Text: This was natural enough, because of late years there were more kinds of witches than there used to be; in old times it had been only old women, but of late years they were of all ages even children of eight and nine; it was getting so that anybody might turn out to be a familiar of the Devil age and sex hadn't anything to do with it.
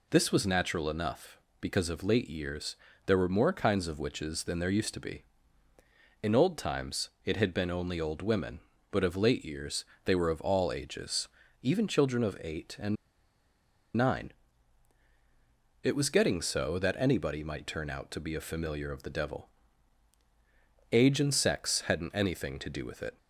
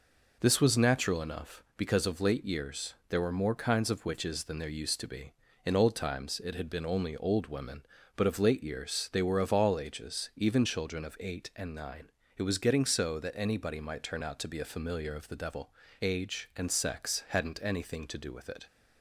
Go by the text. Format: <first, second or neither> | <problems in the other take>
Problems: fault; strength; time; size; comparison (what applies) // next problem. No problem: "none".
second | pauses between "years" and "there"; slight; at 2.7 s; 0.28 s long // pauses between "times" and "it"; slight; at 7.1 s; 0.16 s long // pauses between "years" and "they"; slight; at 9.8 s; 0.22 s long // pauses between "ages" and "even"; slight; at 11.2 s; 0.32 s long // pauses between "and" and "nine"; at 12.9 s; 1.0 s long // pauses between "Devil" and "age"; strong; at 19.4 s; 1.4 s long; slight in the second